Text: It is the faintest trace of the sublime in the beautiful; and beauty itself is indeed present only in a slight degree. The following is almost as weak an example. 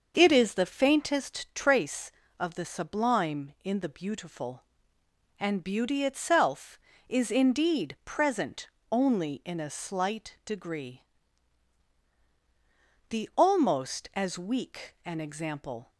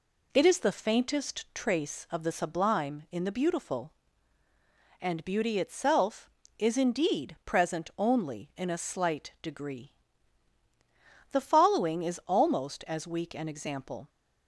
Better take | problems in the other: second | starts louder than the rest; until 1.1 s; 6.5 dB // pauses between "present" and "only"; slight; at 8.6 s; 0.22 s long // skips "following is"; at 13.3 s

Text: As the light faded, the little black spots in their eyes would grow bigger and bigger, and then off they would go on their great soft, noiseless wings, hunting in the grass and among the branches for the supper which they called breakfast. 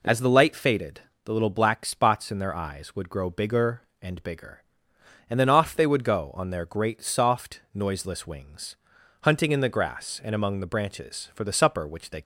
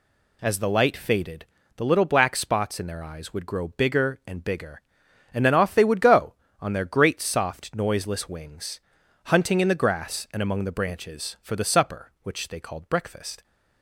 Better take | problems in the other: second | stops before "called breakfast"; at 12.2 s

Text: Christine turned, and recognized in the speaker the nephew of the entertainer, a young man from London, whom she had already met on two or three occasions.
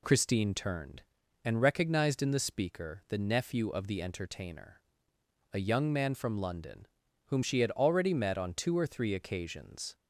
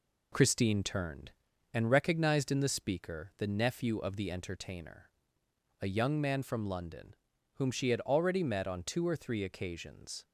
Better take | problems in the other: first | gets quieter; noticeable; throughout; 4 dB

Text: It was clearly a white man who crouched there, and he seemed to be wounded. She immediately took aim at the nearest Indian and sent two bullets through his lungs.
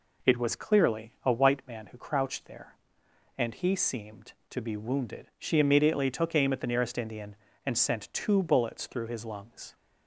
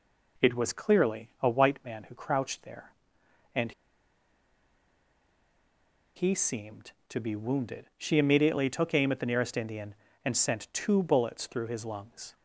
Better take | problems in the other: first | pauses between "and" and "he"; strong; at 3.7 s; 2.4 s long

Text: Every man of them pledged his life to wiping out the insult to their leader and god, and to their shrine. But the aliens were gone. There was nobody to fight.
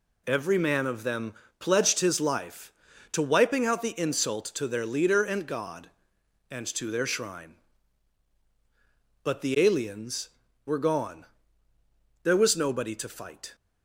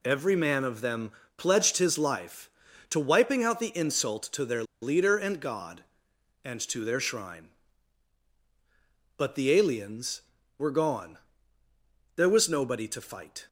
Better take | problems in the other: first | pauses between "them" and "pledged"; slight; at 1.1 s; 0.26 s long; slight in the first // pauses between "their" and "leader"; slight; at 4.6 s; 0.18 s long

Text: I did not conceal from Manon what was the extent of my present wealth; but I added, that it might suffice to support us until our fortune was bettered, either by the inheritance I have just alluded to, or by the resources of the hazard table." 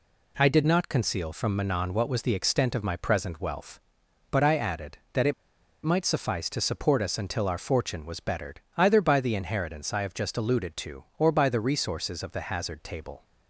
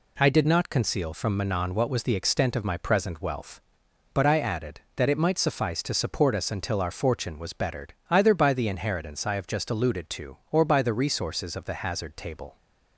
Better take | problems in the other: second | pauses between "it" and "might"; noticeable; at 5.3 s; 0.50 s long

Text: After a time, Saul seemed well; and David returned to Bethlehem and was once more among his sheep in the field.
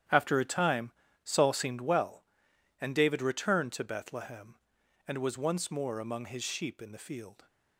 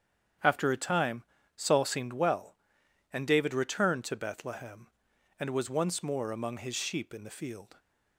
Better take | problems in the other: second | gets quieter; strong; throughout; 12 dB // starts louder than the rest; strong; until 1.4 s; 10.5 dB; strong in the second

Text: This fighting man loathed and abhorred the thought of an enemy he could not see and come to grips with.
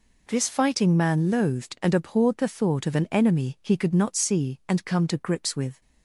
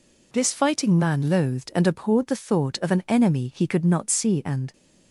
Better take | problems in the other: first | stops before "come to grips with"; at 4.7 s

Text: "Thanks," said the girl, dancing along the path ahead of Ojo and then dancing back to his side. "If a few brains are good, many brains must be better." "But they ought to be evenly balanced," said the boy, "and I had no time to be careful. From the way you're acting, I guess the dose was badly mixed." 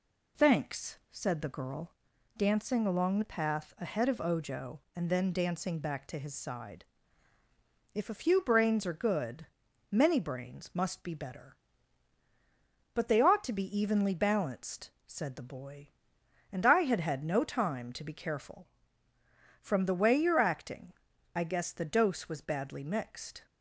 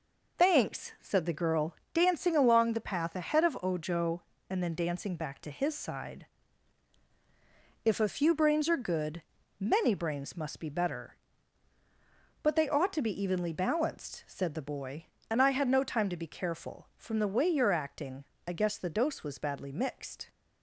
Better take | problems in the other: second | says "had" twice; at 16.9 s

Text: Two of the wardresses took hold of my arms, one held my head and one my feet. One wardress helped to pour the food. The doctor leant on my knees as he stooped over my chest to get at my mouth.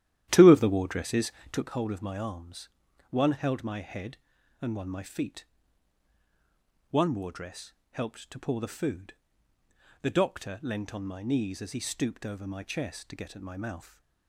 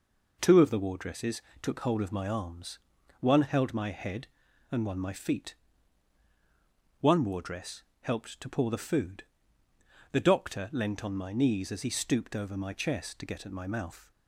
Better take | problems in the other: second | starts louder than the rest; strong; until 1.7 s; 12 dB // pauses between "wardresses" and "took"; slight; at 1.3 s; 0.20 s long; slight in the second // pauses between "wardress" and "helped"; slight; at 7.7 s; 0.20 s long; slight in the second

